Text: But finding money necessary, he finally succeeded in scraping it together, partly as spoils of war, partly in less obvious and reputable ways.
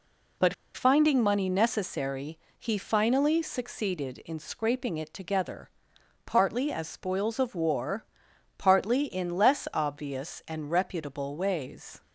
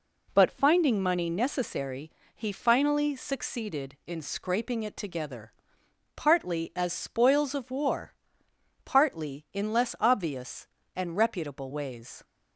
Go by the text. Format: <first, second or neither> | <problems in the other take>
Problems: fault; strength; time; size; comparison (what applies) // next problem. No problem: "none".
second | pauses between "But" and "finding"; slight; at 0.5 s; 0.21 s long